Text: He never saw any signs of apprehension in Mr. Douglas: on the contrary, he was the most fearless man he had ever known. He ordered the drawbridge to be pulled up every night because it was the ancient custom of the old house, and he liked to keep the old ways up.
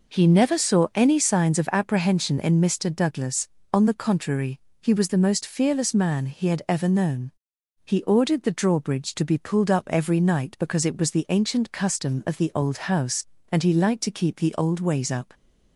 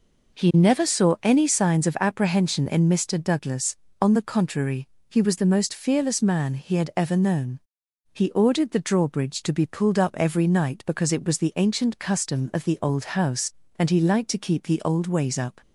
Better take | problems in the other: neither | none

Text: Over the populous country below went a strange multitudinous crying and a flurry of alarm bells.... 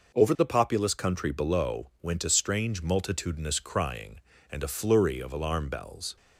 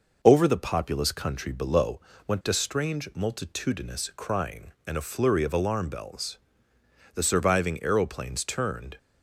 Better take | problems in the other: first | pauses between "below" and "went"; slight; at 1.9 s; 0.26 s long // goes on to say "The surviving aeroplanes turned"; strong; from 7.1 s on; 1.8 s long

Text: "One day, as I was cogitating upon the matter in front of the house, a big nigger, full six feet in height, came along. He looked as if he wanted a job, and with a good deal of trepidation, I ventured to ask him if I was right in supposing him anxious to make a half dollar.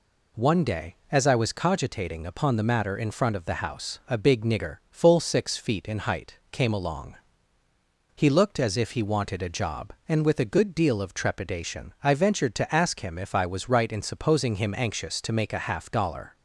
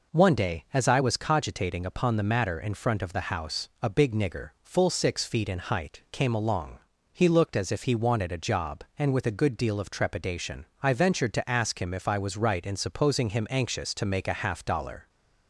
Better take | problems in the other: neither | none

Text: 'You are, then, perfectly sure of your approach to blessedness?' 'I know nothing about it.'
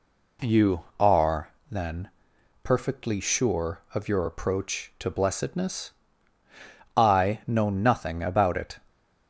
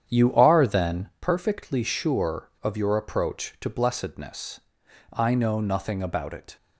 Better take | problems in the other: first | starts louder than the rest; strong; until 1.3 s; 9 dB

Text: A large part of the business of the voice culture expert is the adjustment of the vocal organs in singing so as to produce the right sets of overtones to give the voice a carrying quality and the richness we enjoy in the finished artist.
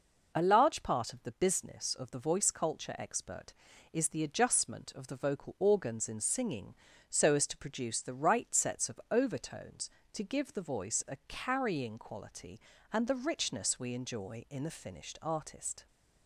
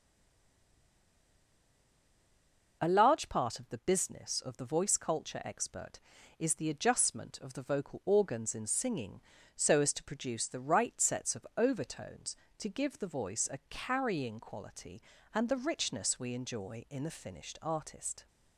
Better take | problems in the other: first | stays silent before the first word; strong; until 2.8 s; 2.8 s long

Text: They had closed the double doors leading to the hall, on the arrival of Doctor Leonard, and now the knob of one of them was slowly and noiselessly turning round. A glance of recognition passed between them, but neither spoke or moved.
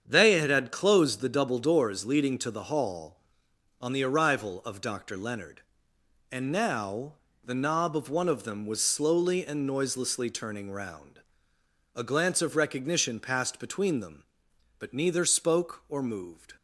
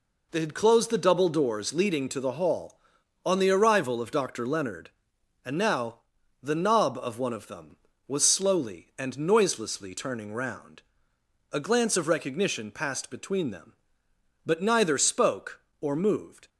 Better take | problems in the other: second | starts louder than the rest; strong; until 1.1 s; 7.5 dB // says "had" twice; at 0.5 s // pauses between "now" and "the"; slight; at 7.1 s; 0.32 s long; also in the second

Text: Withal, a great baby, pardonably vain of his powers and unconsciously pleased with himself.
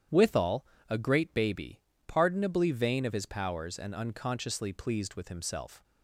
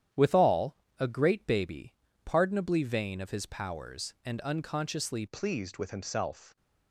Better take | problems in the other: first | starts louder than the rest; strong; until 1.3 s; 10 dB; strong in the first // changes voice at "pleased"; from 5.2 s on; 1.3 s long

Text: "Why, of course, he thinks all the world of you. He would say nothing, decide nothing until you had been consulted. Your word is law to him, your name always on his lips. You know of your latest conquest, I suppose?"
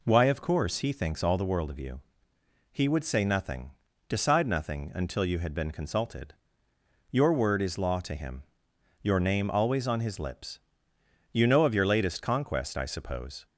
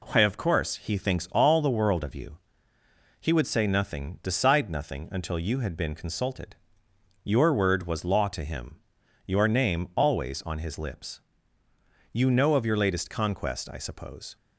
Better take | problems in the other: first | says "was" for "is"; at 7.8 s

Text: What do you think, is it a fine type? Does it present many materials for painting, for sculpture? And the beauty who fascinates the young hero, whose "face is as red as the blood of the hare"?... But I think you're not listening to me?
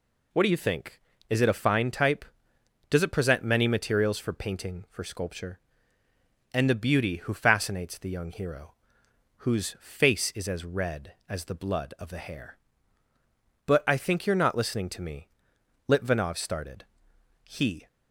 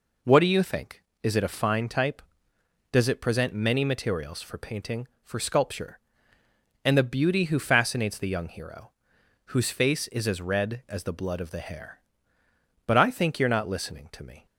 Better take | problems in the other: second | goes on to say "Litvinov started He"; strong; from 15.8 s on; 1.9 s long

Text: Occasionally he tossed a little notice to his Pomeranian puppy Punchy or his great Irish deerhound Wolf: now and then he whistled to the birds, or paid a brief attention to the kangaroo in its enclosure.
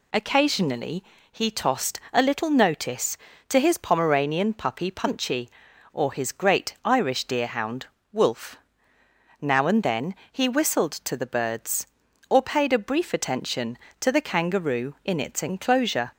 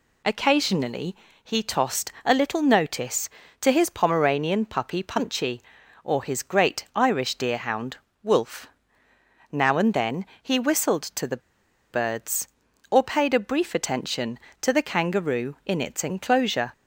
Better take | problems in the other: first | pauses between "Occasionally" and "he"; slight; at 1.1 s; 0.28 s long; slight in the first // pauses between "deerhound" and "Wolf"; slight; at 7.9 s; 0.26 s long; slight in the first // pauses between "then" and "he"; slight; at 10.2 s; 0.16 s long; slight in the first // pauses between "the" and "birds"; noticeable; at 11.4 s; 0.50 s long

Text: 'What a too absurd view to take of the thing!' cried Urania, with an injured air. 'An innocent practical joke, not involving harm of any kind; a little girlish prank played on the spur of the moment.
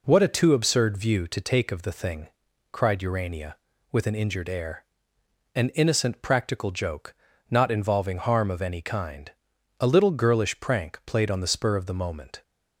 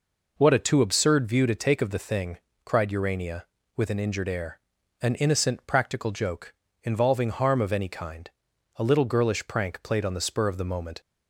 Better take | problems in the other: first | skips "not"; at 6.6 s

